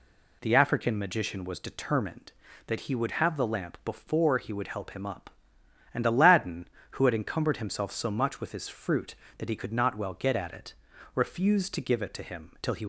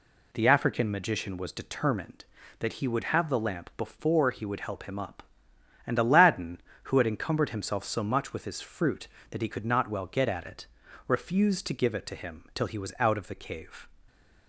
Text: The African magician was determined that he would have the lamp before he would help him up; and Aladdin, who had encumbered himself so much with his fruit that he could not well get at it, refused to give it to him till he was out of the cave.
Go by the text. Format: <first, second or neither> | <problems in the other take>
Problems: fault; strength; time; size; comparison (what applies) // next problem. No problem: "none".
second | stops before "was out of the cave"; at 12.8 s